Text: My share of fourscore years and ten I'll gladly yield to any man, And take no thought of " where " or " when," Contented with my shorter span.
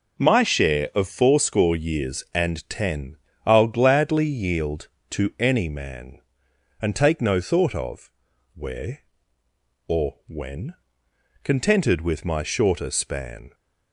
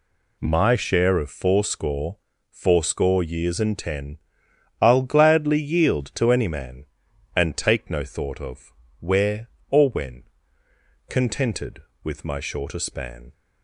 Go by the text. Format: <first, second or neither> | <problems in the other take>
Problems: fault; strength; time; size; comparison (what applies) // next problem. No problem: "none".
first | says "fourscore" twice; at 2.5 s // pauses between "ten" and "I'll"; noticeable; at 4.1 s; 0.64 s long; slight in the first